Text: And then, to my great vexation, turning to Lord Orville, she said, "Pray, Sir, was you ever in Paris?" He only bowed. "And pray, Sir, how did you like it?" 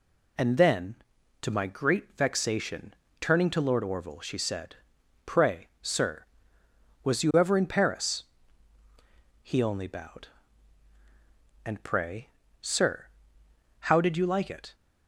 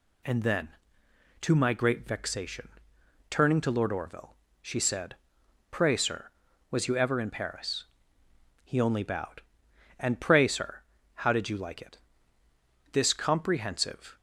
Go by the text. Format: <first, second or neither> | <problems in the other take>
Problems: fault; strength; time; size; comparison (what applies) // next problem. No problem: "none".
first | goes on to say "This comprehensive"; noticeable; from 12.9 s on; 1.2 s long